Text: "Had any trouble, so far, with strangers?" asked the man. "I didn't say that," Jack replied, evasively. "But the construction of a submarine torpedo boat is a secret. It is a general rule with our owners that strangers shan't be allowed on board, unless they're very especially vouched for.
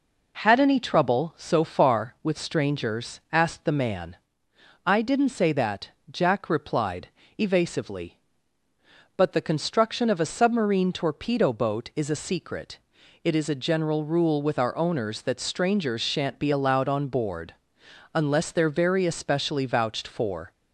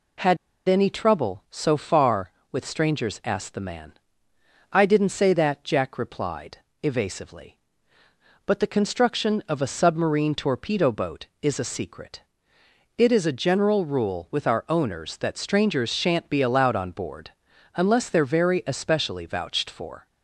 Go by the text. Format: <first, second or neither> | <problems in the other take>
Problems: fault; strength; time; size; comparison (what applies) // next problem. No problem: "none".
first | pauses between "Had" and "any"; slight; at 0.3 s; 0.29 s long